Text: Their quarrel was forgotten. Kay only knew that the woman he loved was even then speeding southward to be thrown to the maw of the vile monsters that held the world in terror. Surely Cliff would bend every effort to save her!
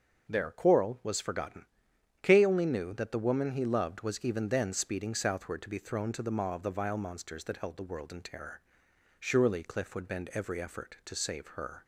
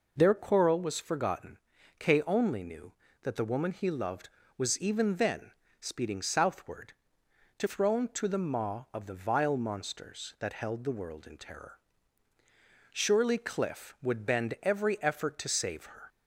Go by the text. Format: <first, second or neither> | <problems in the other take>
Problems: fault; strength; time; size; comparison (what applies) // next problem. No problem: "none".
first | pauses between "then" and "speeding"; slight; at 5.5 s; 0.28 s long // skips "be"; at 7.6 s